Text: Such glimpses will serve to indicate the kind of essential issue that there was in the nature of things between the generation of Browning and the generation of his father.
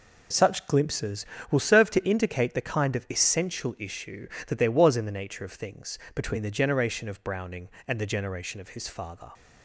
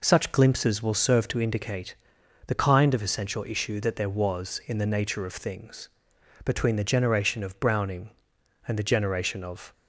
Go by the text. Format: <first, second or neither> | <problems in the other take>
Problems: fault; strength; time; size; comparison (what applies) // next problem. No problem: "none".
first | pauses between "indicate" and "the"; noticeable; at 1.9 s; 0.54 s long // pauses between "things" and "between"; noticeable; at 5.8 s; 0.56 s long; slight in the first // stops before "his father"; at 9.7 s